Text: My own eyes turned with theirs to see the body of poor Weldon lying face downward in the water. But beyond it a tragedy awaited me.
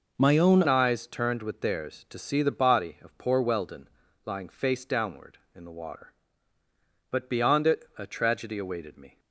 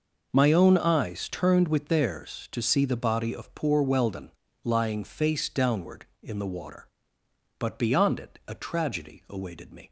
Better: second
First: changes voice at "eyes"; from 0.6 s on; 8.5 s long // pauses between "Weldon" and "lying"; at 3.8 s; 0.38 s long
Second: pauses between "Weldon" and "lying"; slight; at 4.2 s; 0.32 s long

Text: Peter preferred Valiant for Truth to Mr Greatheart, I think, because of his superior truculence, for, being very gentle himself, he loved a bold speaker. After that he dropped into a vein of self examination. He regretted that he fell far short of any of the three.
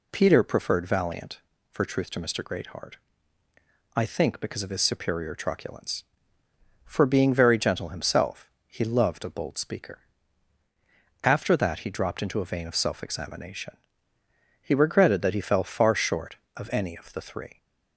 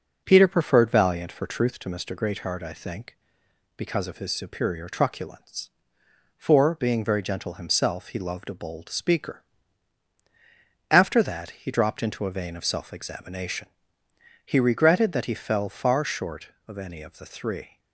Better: first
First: none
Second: starts louder than the rest; noticeable; until 1.8 s; 5.5 dB

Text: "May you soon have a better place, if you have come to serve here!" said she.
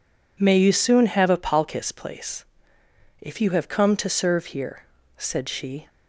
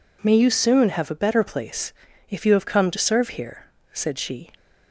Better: second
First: says "palkis" for "better"; at 1.3 s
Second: none

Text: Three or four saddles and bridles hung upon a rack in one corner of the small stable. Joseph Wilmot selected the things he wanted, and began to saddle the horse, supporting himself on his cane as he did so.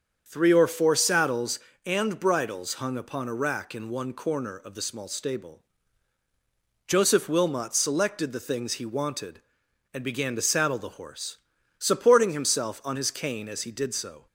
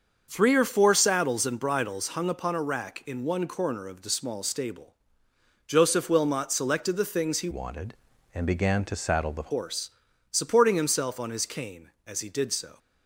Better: first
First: starts louder than the rest; strong; until 1.2 s; 7 dB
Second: starts louder than the rest; until 1.3 s; 6.5 dB // changes voice from "wanted" to "the"; from 7.5 to 9.4 s; 1.9 s long

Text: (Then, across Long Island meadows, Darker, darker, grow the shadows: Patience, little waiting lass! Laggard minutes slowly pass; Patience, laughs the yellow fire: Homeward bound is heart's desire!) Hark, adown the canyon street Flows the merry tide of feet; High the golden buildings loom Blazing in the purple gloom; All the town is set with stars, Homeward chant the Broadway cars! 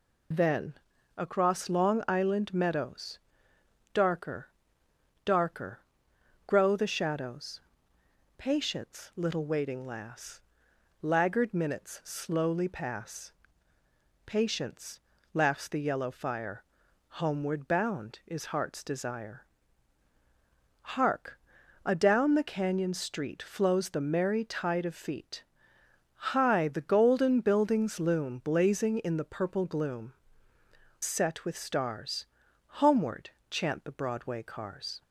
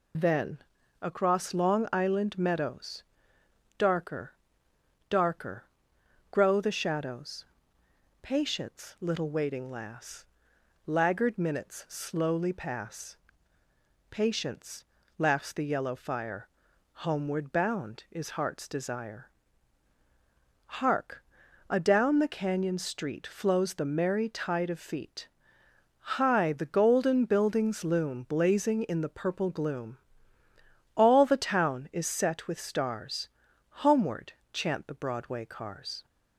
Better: second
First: skips "All the town is"; at 30.5 s // pauses between "Homeward" and "chant"; slight; at 33.2 s; 0.22 s long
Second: pauses between "Homeward" and "chant"; slight; at 34.3 s; 0.22 s long

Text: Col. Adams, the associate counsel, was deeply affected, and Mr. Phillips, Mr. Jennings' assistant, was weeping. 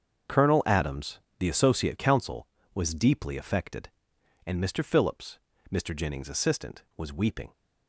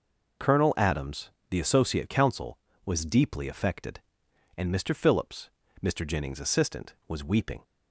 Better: second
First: gets quieter; strong; throughout; 13 dB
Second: none

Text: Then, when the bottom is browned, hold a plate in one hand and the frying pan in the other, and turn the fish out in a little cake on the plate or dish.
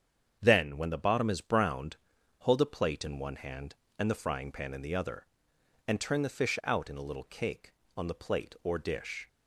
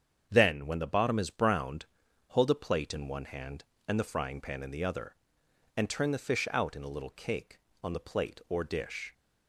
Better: neither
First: starts louder than the rest; strong; until 1.4 s; 7.5 dB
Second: starts louder than the rest; strong; until 1.3 s; 7.5 dB

